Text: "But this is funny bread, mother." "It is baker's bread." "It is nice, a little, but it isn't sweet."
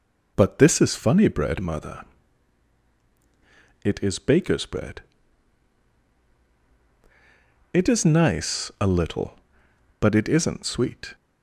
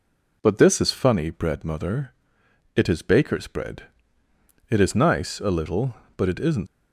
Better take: first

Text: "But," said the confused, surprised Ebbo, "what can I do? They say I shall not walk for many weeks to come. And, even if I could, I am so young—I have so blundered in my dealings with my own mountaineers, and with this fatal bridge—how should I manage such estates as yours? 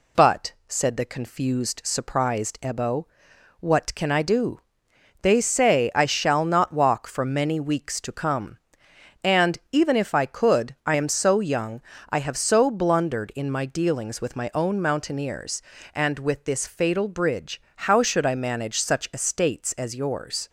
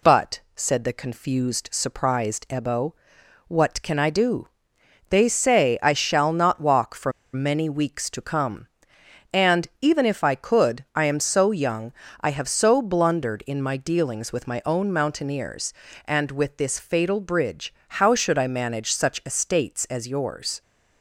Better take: first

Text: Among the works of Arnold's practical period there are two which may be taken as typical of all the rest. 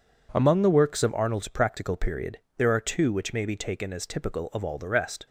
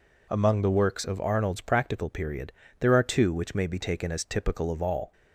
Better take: first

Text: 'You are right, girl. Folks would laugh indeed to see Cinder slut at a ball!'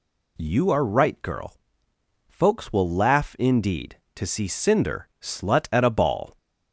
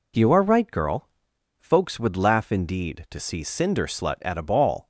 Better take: second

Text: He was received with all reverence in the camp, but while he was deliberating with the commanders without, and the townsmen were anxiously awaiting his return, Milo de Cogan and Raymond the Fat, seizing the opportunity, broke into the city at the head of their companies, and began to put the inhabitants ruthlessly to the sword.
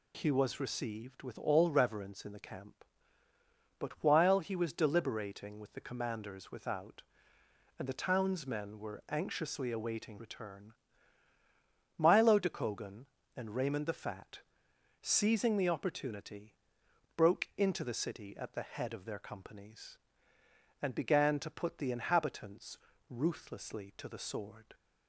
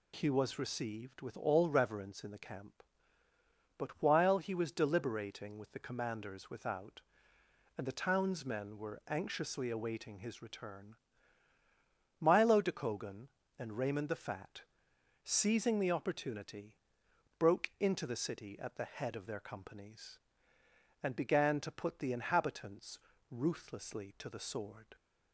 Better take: second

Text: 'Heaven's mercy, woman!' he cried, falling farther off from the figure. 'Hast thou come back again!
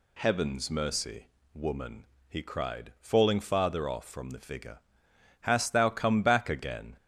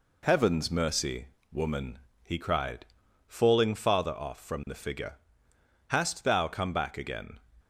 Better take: second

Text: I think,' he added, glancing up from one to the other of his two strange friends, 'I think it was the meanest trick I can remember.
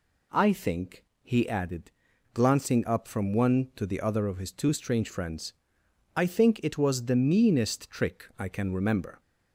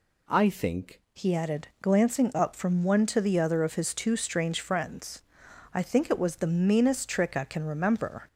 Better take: first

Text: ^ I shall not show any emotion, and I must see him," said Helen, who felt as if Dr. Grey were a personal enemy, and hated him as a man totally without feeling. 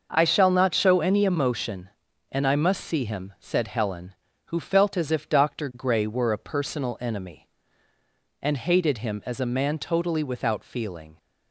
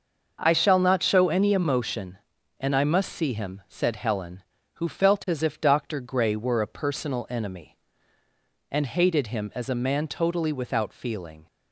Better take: neither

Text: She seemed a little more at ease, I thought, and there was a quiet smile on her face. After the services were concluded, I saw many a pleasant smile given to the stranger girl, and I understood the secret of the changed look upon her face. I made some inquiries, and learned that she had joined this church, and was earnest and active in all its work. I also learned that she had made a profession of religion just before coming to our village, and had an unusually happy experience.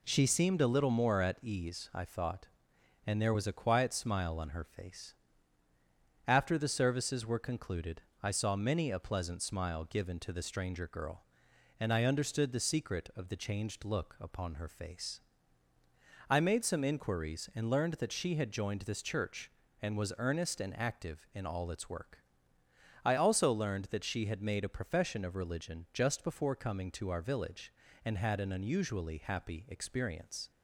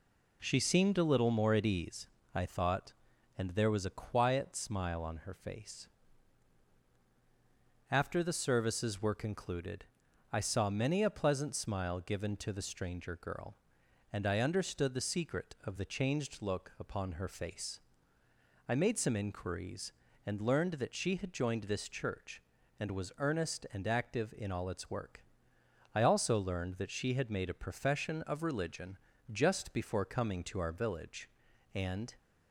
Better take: first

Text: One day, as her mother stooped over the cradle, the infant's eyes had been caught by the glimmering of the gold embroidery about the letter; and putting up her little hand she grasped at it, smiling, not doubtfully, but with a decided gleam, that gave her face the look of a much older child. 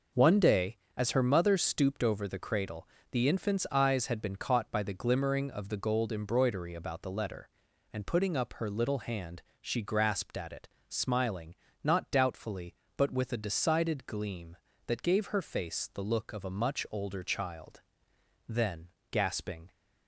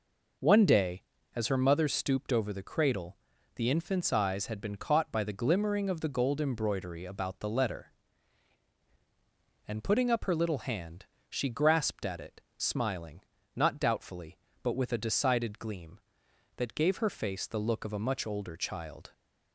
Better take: second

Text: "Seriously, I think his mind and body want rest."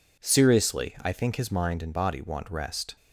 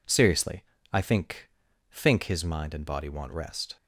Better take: first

